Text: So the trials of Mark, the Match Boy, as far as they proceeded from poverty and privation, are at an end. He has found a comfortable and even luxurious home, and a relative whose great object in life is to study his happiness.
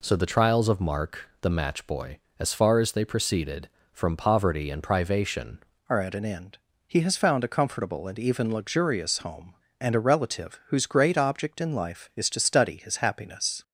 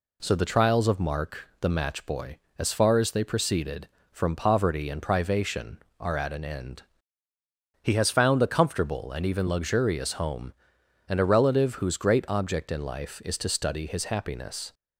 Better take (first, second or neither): second